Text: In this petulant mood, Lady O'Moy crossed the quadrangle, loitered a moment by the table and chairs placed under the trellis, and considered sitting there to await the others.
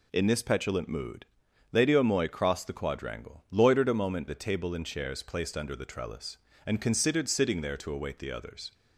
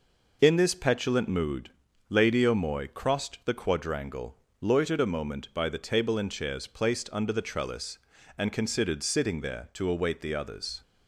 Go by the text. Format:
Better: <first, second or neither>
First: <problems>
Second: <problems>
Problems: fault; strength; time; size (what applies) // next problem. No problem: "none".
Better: second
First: skips "by"; at 4.2 s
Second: none